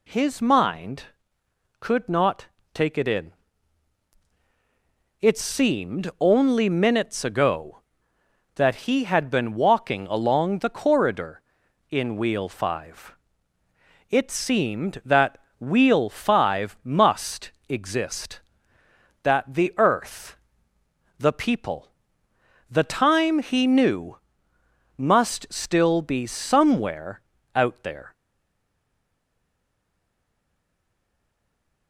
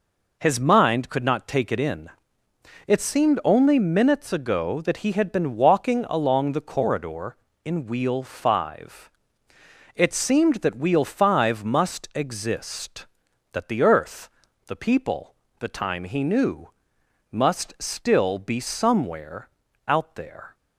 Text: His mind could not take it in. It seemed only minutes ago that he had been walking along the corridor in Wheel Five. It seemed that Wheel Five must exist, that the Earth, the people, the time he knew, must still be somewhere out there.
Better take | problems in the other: second | pauses between "not" and "take"; slight; at 2.4 s; 0.28 s long // pauses between "that" and "Wheel"; slight; at 15.3 s; 0.20 s long // pauses between "must" and "exist"; slight; at 17.5 s; 0.16 s long // pauses between "somewhere" and "out"; at 27.1 s; 0.38 s long; also in the second // stays silent after the last word; strong; from 28.1 s on; 3.7 s long

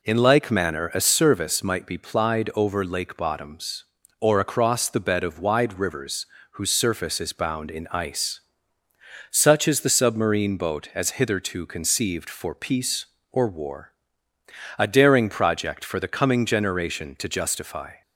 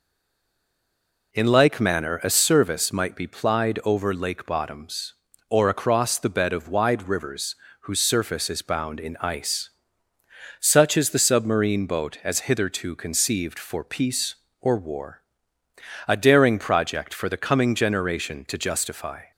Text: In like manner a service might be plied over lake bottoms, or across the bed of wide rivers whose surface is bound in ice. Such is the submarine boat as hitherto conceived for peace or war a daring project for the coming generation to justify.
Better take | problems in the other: first | stays silent before the first word; noticeable; until 1.3 s; 1.3 s long // pauses between "rivers" and "whose"; slight; at 7.5 s; 0.28 s long; slight in the first // pauses between "war" and "a"; noticeable; at 15.1 s; 0.88 s long; noticeable in the first

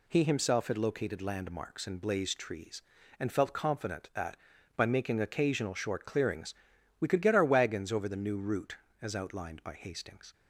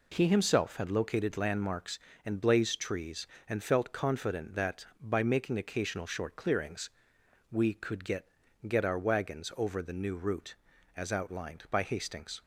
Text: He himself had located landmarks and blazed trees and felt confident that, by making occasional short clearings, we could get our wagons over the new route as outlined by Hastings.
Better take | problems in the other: first | says "get" twice; at 8.6 s

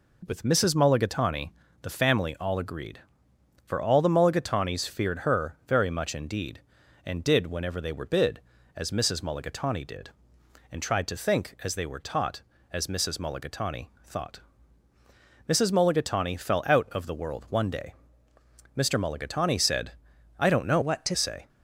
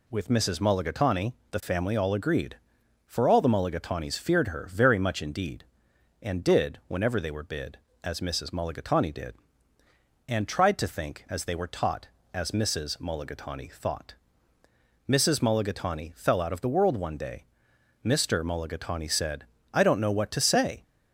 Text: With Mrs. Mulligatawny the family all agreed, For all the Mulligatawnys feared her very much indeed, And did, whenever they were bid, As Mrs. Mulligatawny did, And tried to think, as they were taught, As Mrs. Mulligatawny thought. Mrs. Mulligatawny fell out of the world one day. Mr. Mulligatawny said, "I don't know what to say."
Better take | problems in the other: second | pauses between "Mulligatawny" and "the"; slight; at 1.4 s; 0.32 s long; slight in the second // changes voice from "what" to "to"; from 20.8 to 21.1 s; 0.3 s long

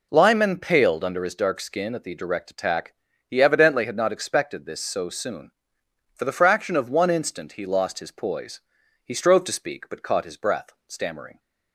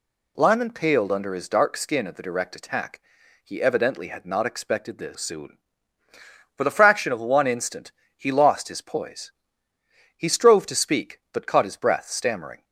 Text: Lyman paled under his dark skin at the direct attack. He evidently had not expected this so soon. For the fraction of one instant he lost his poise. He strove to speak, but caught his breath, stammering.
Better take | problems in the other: first | skips "so"; at 5.1 s // pauses between "instant" and "he"; slight; at 7.9 s; 0.24 s long

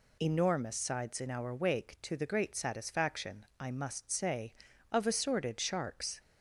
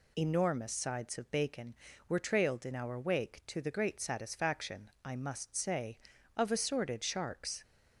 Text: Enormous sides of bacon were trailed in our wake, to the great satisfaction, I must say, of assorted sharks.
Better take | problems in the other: second | skips "of bacon were trailed"; at 1.2 s

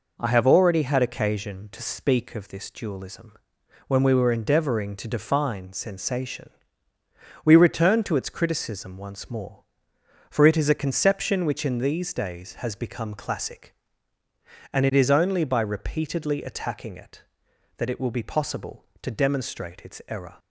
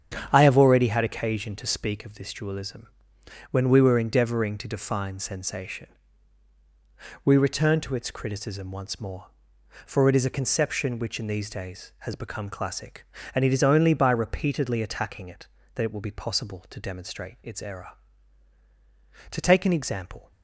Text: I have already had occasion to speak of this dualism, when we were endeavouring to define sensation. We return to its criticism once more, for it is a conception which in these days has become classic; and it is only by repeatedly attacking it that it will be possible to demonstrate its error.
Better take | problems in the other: first | starts louder than the rest; strong; until 1.3 s; 8 dB // goes on to say "To take an example"; noticeable; from 19.2 s on; 1.0 s long

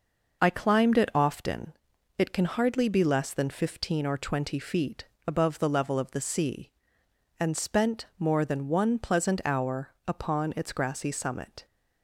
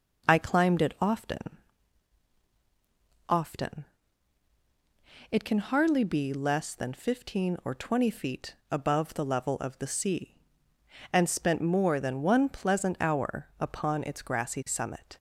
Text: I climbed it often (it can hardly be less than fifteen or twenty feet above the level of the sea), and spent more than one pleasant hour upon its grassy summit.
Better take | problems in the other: first | says "often" twice; at 3.2 s // pauses between "feet" and "above"; slight; at 8.5 s; 0.16 s long; slight in the first

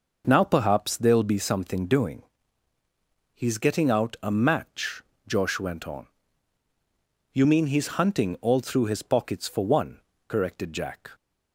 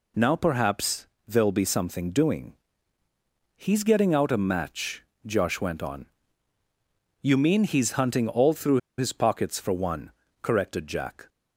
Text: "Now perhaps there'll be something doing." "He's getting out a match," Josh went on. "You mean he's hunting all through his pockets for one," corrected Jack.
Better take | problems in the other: first | pauses between "perhaps" and "there'll"; slight; at 1.0 s; 0.20 s long // pauses between "through" and "his"; slight; at 8.7 s; 0.19 s long

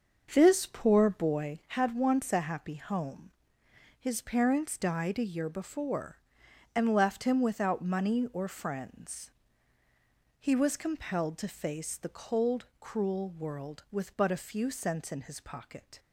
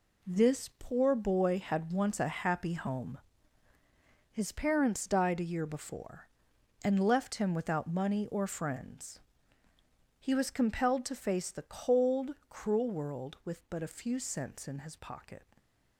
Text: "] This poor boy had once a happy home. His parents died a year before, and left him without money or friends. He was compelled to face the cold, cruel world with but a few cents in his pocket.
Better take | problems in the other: second | starts louder than the rest; until 1.5 s; 6.5 dB

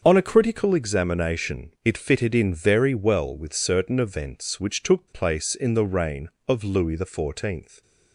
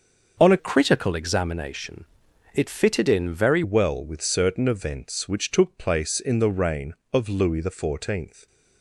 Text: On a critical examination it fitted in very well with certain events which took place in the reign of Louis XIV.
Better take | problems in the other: first | starts louder than the rest; until 1.4 s; 6.5 dB; also in the first // changes voice from "critical" to "very"; from 0.5 to 3.6 s; 3.1 s long // pauses between "examination" and "it"; noticeable; at 2.0 s; 0.50 s long

